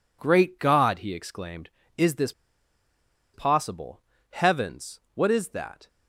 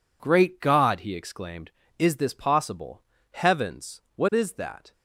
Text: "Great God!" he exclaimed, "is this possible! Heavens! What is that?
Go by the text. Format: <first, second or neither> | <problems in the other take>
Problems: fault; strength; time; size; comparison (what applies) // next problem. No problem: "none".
second | pauses between "this" and "possible"; at 2.3 s; 1.0 s long